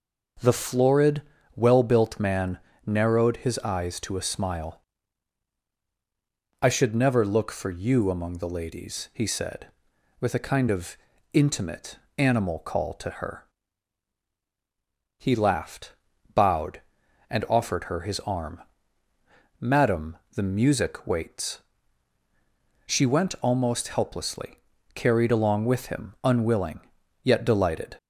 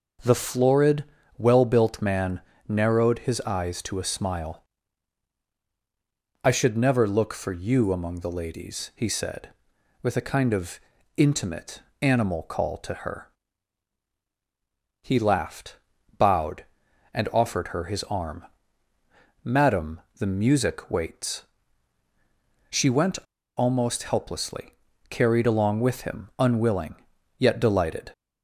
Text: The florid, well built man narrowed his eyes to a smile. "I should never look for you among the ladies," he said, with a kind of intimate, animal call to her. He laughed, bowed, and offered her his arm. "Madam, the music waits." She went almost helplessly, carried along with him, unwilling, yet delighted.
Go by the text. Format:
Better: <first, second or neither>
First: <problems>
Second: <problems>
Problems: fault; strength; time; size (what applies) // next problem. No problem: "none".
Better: first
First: pauses between "man" and "narrowed"; slight; at 2.5 s; 0.26 s long // pauses between "of" and "intimate"; at 10.9 s; 0.37 s long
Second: pauses between "man" and "narrowed"; slight; at 2.4 s; 0.26 s long // pauses between "of" and "intimate"; at 10.7 s; 0.38 s long // pauses between "went" and "almost"; at 23.1 s; 0.39 s long